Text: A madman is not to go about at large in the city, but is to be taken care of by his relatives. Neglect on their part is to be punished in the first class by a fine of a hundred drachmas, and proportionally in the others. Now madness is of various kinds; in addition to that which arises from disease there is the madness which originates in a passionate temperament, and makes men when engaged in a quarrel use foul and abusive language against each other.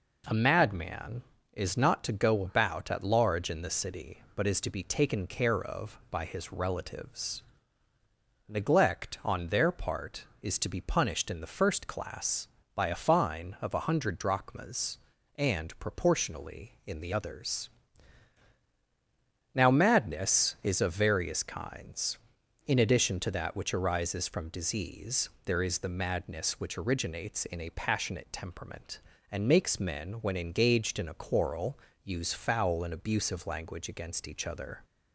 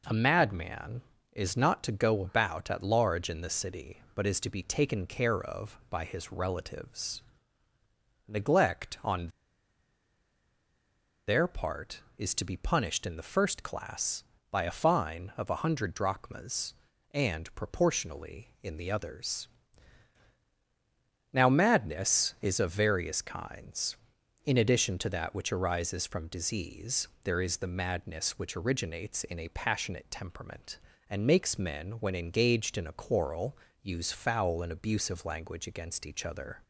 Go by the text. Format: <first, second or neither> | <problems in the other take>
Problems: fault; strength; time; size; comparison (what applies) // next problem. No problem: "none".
first | pauses between "on" and "their"; strong; at 9.2 s; 1.9 s long // pauses between "disease" and "there"; slight; at 27.0 s; 0.16 s long; slight in the first // pauses between "quarrel" and "use"; slight; at 33.5 s; 0.26 s long; slight in the first